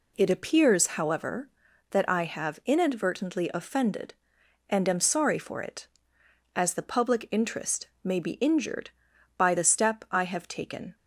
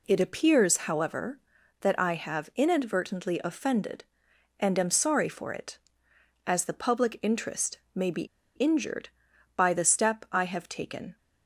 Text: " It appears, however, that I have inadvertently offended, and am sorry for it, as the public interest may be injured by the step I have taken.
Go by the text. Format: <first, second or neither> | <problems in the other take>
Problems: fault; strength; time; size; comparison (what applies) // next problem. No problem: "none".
first | pauses between "interest" and "may"; slight; at 7.7 s; 0.16 s long; slight in the first // pauses between "be" and "injured"; slight; at 8.2 s; 0.32 s long